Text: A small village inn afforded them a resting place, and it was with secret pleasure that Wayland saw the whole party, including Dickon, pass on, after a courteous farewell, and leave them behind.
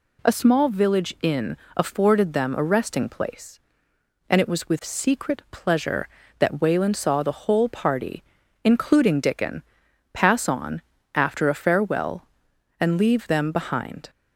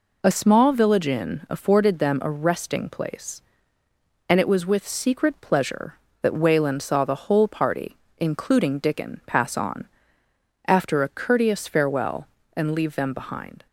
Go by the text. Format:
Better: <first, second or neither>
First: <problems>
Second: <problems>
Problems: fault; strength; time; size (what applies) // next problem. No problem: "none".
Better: second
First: pauses between "inn" and "afforded"; slight; at 1.5 s; 0.22 s long // skips "courteous"; at 11.5 s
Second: none